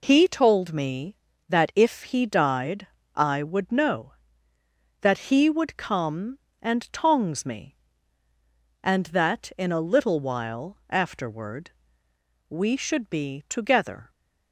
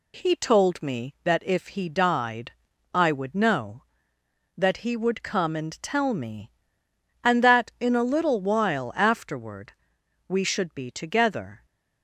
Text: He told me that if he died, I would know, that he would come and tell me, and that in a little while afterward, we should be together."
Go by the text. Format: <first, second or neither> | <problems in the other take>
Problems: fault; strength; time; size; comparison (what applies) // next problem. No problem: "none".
second | says "tongs" for "tell"; at 6.9 s